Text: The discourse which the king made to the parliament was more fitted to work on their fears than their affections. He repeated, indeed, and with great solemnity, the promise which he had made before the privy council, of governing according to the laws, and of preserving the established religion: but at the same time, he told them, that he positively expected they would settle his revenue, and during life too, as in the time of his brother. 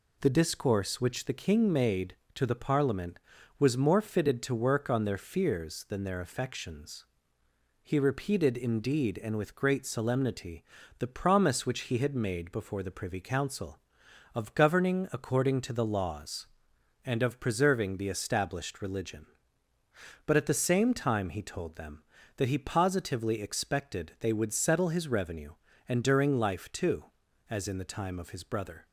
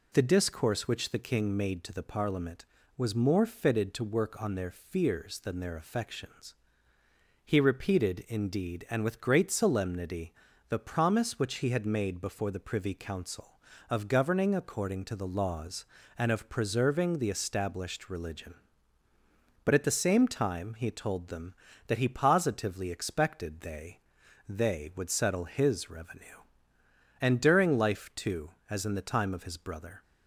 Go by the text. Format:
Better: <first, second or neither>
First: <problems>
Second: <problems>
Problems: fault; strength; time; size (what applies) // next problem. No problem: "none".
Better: first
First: none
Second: says "they" twice; at 24.4 s